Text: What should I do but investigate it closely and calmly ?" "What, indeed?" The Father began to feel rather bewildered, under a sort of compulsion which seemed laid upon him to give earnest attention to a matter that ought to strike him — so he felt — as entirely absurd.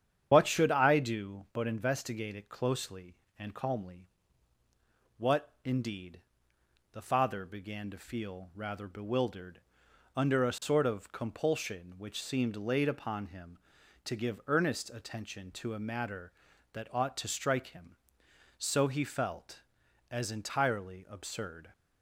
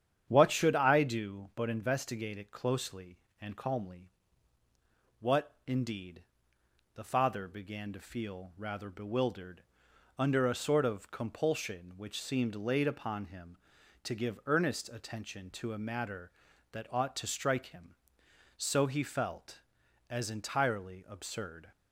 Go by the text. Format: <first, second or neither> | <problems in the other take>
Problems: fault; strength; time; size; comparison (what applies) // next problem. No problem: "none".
second | loses the start of "What"; at 0.3 s; 70 ms // starts louder than the rest; strong; until 1.3 s; 9.5 dB; strong in the second